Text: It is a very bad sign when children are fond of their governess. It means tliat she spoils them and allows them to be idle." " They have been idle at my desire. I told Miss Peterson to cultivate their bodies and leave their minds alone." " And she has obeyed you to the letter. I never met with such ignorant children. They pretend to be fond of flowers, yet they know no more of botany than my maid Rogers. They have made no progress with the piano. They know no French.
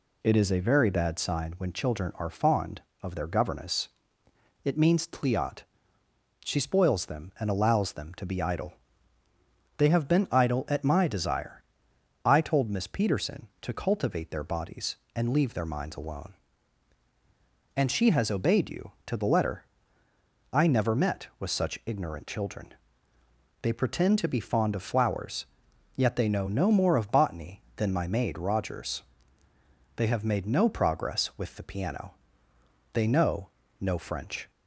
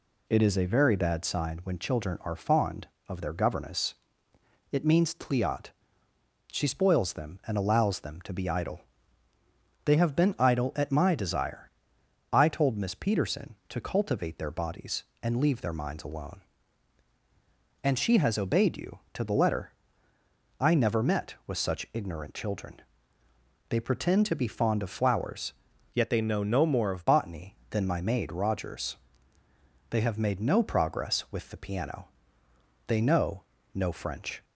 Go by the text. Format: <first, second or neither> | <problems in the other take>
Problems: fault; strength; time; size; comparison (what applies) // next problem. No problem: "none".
first | pauses between "tliat" and "she"; noticeable; at 5.6 s; 0.84 s long; noticeable in the first // changes voice from "yet" to "of"; from 25.9 to 27.0 s; 1.1 s long // pauses between "know" and "no"; slight; at 33.4 s; 0.32 s long; slight in the first